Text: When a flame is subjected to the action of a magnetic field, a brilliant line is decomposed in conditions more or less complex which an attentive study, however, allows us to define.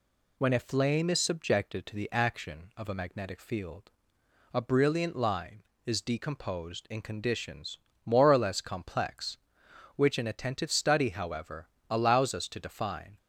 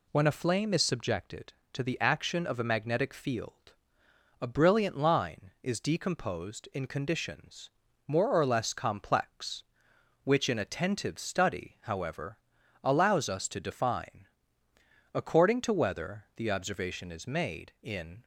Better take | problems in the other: first | pauses between "conditions" and "more"; slight; at 7.6 s; 0.36 s long; slight in the first // goes on to say "According to whether the observation is made in"; strong; from 15.1 s on; 3.1 s long

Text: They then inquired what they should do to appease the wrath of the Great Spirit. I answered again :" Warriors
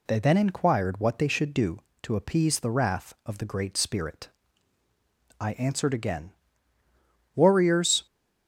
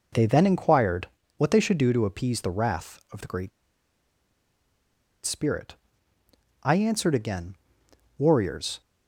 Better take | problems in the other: first | pauses between "inquired" and "what"; slight; at 1.0 s; 0.30 s long // pauses between "Great" and "Spirit"; strong; at 3.5 s; 1.7 s long

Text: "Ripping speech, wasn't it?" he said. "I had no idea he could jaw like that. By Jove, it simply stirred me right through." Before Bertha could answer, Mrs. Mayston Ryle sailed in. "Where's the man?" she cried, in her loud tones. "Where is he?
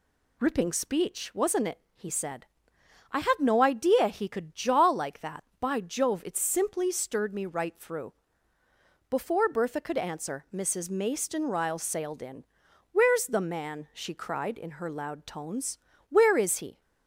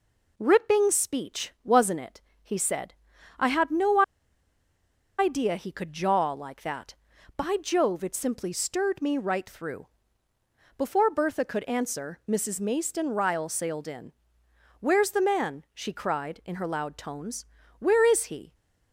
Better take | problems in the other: first | pauses between "no" and "idea"; at 4.0 s; 1.1 s long

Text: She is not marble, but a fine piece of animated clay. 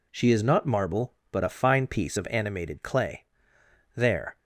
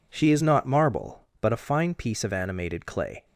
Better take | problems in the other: second | goes on to say "There"; slight; from 3.9 s on; 0.44 s long

